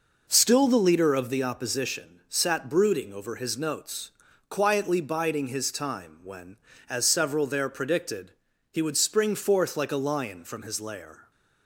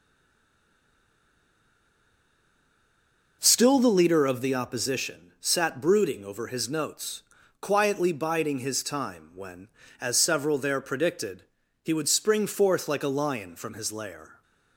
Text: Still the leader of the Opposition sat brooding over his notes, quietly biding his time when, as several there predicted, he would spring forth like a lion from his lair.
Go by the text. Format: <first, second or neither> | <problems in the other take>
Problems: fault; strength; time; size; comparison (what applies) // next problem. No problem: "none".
first | stays silent before the first word; strong; until 3.3 s; 3.3 s long